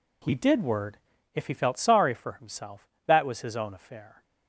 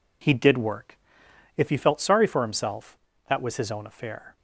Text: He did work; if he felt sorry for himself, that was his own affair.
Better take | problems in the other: second | says "word" for "work"; at 0.6 s

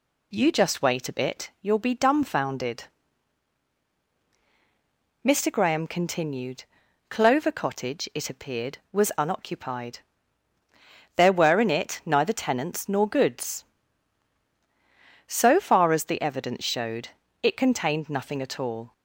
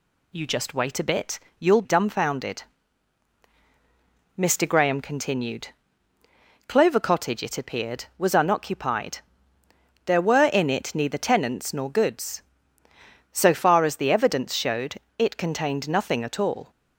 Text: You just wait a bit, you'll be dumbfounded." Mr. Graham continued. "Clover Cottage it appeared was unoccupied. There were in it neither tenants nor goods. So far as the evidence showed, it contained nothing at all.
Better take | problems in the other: first | skips "be"; at 1.8 s

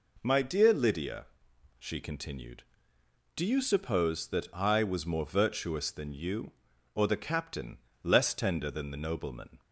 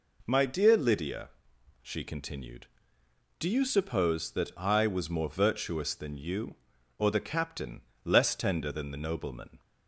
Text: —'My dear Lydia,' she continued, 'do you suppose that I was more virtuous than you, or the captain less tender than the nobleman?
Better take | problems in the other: neither | pauses between "captain" and "less"; slight; the same in both

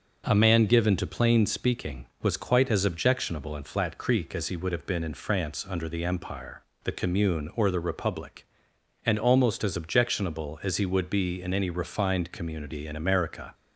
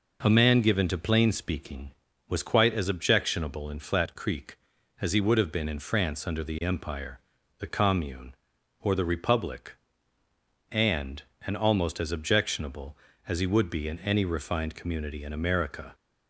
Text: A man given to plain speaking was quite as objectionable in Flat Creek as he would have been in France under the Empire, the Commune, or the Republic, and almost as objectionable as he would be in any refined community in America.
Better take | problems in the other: first | says "and" twice; at 11.4 s

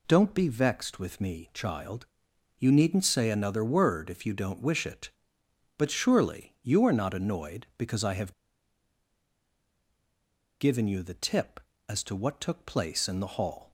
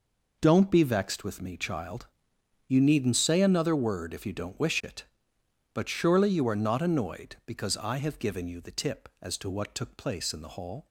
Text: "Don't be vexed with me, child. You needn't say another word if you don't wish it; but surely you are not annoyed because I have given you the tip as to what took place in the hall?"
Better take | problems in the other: second | pauses between "have" and "given"; strong; at 8.3 s; 2.2 s long

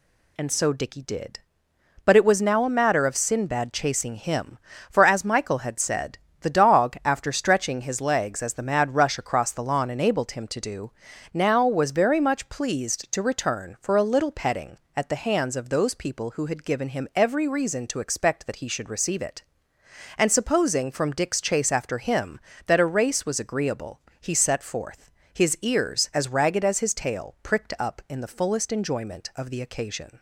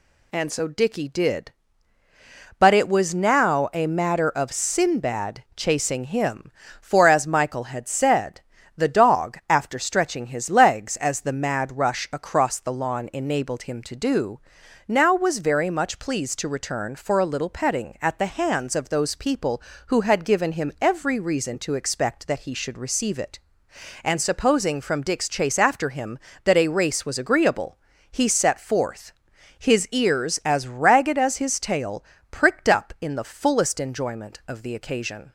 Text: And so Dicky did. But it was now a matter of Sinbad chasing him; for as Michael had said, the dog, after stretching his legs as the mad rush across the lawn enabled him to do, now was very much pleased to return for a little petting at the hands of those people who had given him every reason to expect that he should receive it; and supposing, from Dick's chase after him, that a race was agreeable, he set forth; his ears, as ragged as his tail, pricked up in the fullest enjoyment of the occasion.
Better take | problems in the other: neither | none

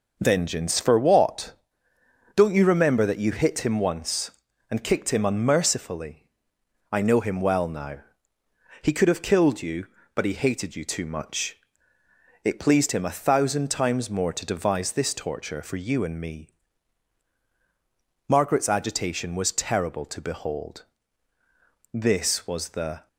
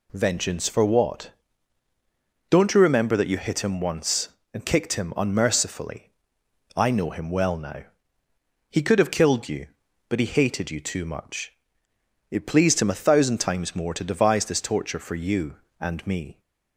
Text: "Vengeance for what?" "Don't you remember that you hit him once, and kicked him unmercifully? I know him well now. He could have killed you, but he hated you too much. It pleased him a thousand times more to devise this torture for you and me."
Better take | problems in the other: second | goes on to say "Margaret's agitation was terrible to behold This was the"; strong; from 18.2 s on; 4.8 s long

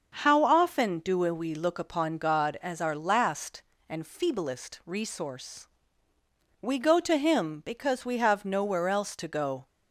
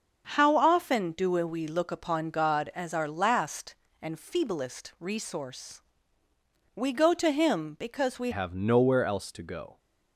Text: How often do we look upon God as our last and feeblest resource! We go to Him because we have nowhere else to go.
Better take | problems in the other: first | starts louder than the rest; until 1.3 s; 6.5 dB; also in the first // changes voice at "have"; from 8.3 s on; 1.4 s long

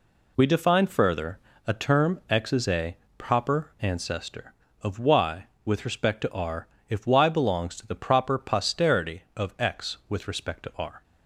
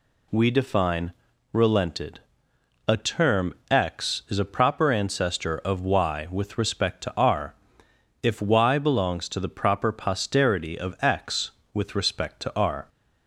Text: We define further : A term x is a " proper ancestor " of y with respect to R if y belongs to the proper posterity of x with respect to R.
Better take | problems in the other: first | says "relented" for "further"; at 1.5 s // pauses between "term" and "x"; slight; at 3.5 s; 0.16 s long // pauses between "R" and "if"; noticeable; at 7.5 s; 0.68 s long; slight in the first

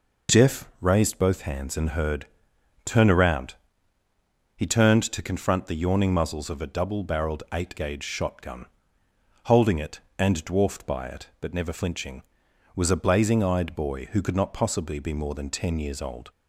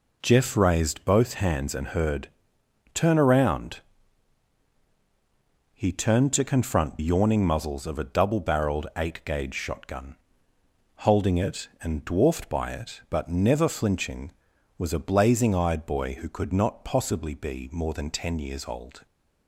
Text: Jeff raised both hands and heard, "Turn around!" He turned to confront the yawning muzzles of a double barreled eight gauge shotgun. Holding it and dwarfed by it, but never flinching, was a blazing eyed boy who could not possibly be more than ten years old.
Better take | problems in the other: first | skips "the"; at 6.9 s

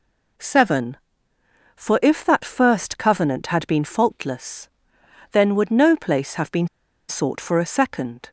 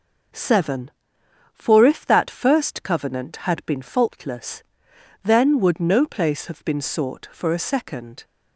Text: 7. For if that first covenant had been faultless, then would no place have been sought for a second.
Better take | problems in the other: second | pauses between "been" and "sought"; at 6.6 s; 0.40 s long

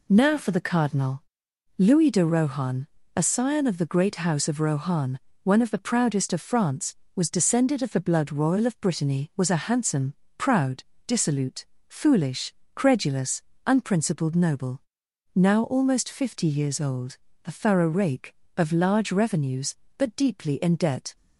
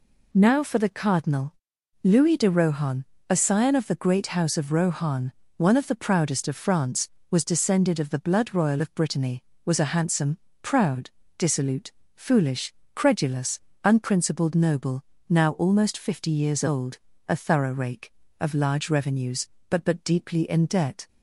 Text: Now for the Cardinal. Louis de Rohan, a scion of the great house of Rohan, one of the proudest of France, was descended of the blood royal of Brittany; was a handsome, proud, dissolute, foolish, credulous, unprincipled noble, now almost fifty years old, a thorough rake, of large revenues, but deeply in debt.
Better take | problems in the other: first | says "but" twice; at 19.8 s

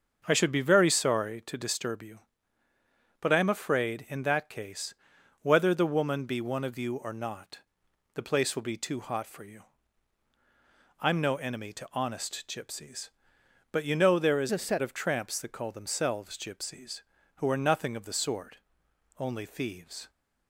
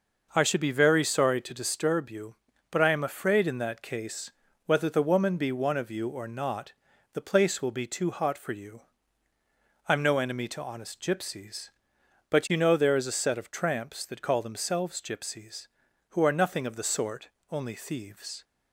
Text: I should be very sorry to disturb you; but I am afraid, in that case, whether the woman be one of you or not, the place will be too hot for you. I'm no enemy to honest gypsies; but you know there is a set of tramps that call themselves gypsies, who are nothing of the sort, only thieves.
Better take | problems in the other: second | starts louder than the rest; until 1.2 s; 7 dB // changes voice from "a" to "set"; from 14.5 to 14.8 s; 0.3 s long

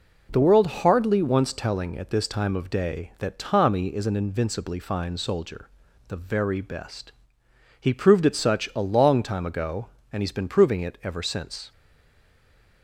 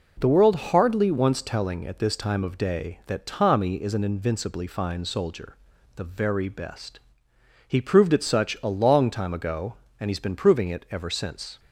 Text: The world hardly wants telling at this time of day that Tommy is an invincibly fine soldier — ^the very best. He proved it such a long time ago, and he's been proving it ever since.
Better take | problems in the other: second | stays silent after the last word; from 11.7 s on; 1.1 s long

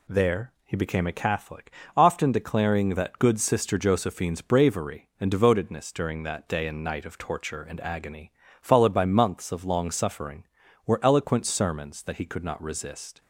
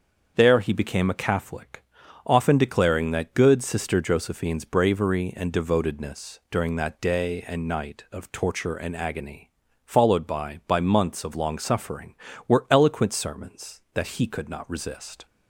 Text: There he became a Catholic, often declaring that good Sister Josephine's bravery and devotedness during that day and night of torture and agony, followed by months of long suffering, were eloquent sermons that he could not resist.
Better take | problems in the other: first | starts louder than the rest; until 1.3 s; 7 dB // says "by" twice; at 10.6 s

